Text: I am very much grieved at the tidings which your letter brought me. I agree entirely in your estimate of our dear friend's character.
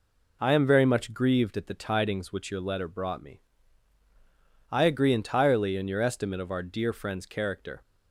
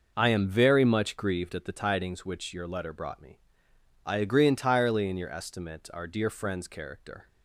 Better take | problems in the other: first | skips "of"; at 5.9 s

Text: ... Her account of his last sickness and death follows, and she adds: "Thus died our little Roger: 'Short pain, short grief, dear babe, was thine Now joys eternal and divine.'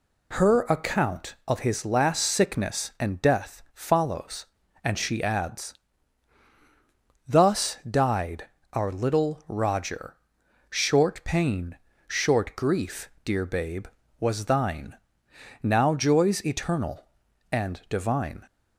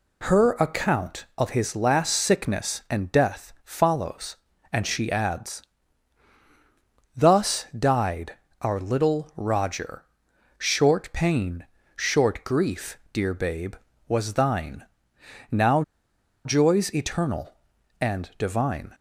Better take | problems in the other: first | pauses between "died" and "our"; slight; at 8.3 s; 0.26 s long; slight in the first // pauses between "thine" and "Now"; noticeable; at 14.8 s; 0.64 s long; noticeable in the first // pauses between "Now" and "joys"; noticeable; at 15.8 s; 0.63 s long

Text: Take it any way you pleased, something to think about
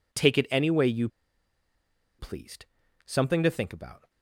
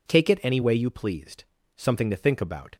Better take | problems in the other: second | pauses between "you" and "pleased"; at 1.0 s; 1.1 s long

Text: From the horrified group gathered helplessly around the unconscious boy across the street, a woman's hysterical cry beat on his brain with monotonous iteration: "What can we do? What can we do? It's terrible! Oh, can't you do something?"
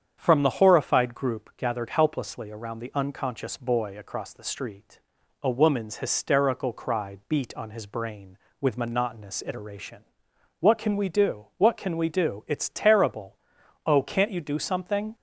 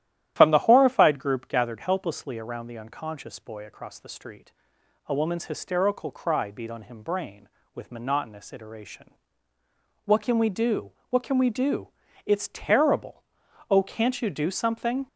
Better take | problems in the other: first | starts louder than the rest; strong; until 1.3 s; 12.5 dB; strong in the first // says "him" for "his"; at 6.8 s

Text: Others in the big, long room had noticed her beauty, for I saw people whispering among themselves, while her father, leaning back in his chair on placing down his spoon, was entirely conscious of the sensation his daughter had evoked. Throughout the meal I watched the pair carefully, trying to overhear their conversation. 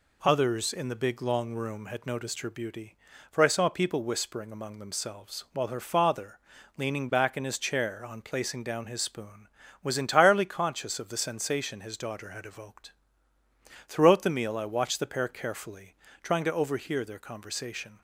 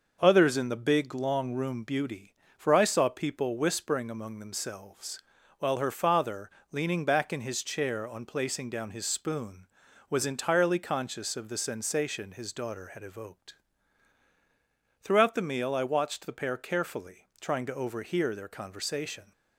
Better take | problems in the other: first | starts louder than the rest; noticeable; until 1.2 s; 6 dB // skips "had noticed her"; at 1.8 s

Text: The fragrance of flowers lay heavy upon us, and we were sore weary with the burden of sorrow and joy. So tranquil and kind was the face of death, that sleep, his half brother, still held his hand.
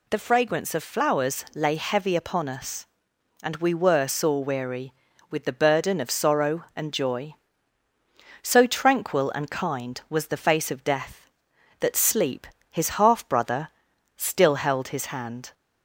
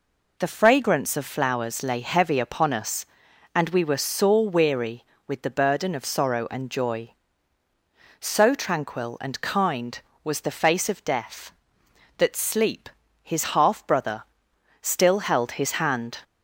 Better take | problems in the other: neither | none

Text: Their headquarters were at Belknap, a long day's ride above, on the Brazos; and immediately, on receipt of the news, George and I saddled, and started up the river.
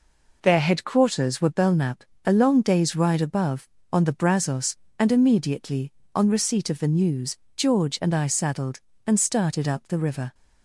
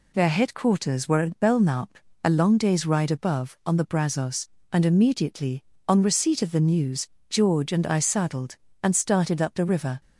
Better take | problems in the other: second | skips "at"; at 1.4 s

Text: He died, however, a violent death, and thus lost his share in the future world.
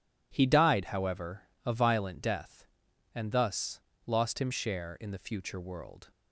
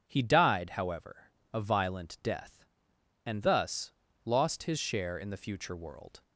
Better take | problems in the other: second | pauses between "thus" and "lost"; slight; at 3.8 s; 0.26 s long; slight in the second // says "him" for "his"; at 4.3 s

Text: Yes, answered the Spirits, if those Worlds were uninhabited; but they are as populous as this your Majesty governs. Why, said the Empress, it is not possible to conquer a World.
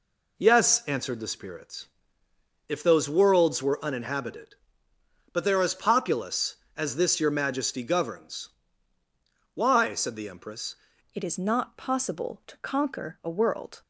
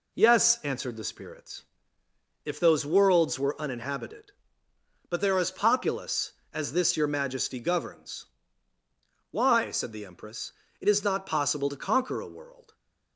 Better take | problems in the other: second | changes voice at "it"; from 11.1 s on; 2.7 s long

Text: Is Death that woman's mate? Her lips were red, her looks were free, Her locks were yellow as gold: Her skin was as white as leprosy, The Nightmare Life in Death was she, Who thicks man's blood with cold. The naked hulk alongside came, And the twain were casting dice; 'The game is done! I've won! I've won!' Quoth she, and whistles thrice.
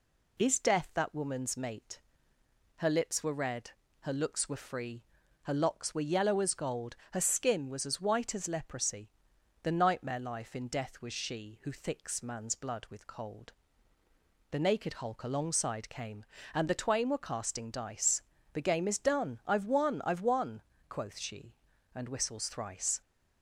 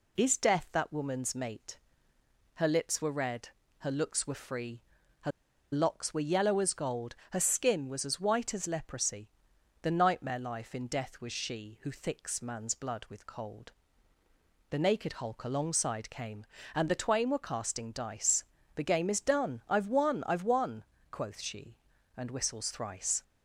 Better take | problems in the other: first | pauses between "Her" and "locks"; at 5.3 s; 0.41 s long

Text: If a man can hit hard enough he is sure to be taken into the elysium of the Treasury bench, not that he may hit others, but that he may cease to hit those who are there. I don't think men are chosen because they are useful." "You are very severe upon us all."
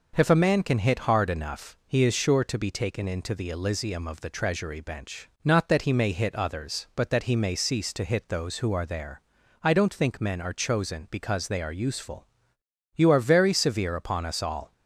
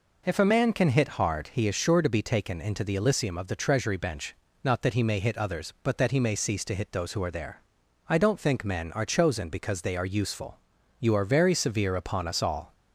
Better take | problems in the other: first | skips "enough"; at 1.4 s

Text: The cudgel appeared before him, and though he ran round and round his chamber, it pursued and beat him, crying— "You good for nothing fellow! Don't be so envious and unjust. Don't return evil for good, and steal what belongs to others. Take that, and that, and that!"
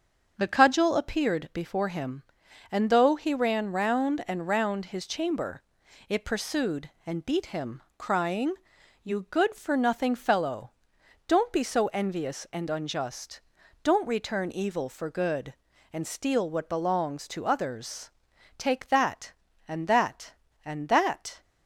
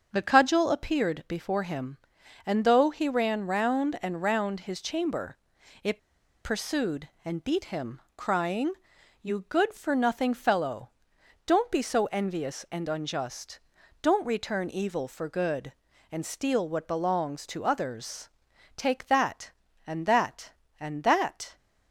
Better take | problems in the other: first | starts louder than the rest; until 1.1 s; 6.5 dB; also in the first // pauses between "it" and "pursued"; at 5.9 s; 0.45 s long

